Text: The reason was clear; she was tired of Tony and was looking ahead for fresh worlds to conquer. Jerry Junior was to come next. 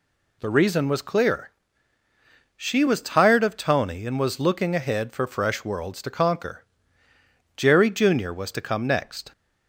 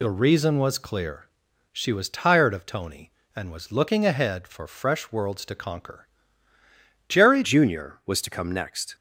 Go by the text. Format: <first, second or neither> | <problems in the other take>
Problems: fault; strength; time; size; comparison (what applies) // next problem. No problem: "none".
first | changes voice at "Junior"; from 7.4 s on; 1.5 s long